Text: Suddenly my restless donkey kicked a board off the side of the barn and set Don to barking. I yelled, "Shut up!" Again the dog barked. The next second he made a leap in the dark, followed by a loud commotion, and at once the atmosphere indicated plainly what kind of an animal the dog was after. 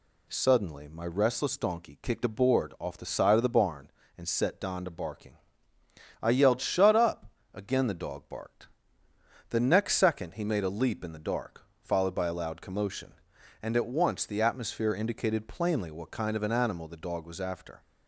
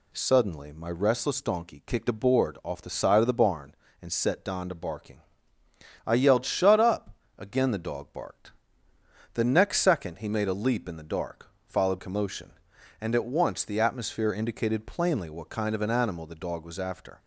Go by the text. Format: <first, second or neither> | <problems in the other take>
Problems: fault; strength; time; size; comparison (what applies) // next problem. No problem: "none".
first | skips "by a loud"; at 11.9 s